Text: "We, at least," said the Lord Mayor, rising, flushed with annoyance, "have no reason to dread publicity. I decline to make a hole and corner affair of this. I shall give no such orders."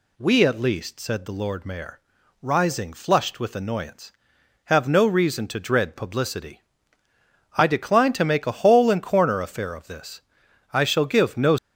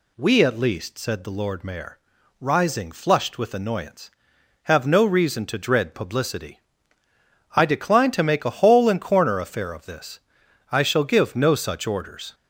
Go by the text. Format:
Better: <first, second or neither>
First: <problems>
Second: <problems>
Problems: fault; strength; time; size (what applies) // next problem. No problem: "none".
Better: second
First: stops before "such orders"; at 11.5 s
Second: none